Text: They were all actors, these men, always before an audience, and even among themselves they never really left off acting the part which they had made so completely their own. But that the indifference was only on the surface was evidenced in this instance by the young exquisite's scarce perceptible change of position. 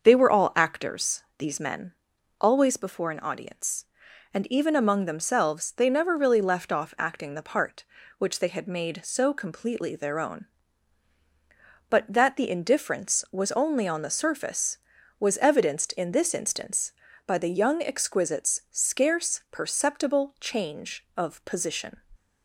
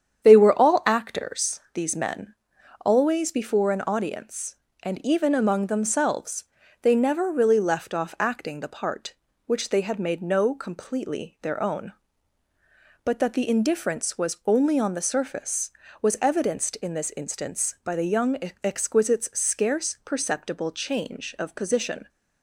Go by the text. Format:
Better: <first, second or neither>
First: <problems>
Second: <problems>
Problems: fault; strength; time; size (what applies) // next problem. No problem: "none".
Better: first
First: starts louder than the rest; until 1.0 s; 6.5 dB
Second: starts louder than the rest; strong; until 1.2 s; 8.5 dB // pauses between "themselves" and "they"; at 6.4 s; 0.38 s long // says "no" for "so"; at 10.2 s // pauses between "young" and "exquisite's"; slight; at 18.3 s; 0.26 s long